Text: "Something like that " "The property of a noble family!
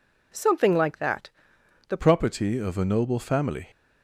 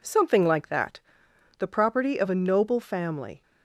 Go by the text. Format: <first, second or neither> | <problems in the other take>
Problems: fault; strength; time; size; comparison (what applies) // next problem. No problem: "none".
second | changes voice at "property"; from 1.9 s on; 1.7 s long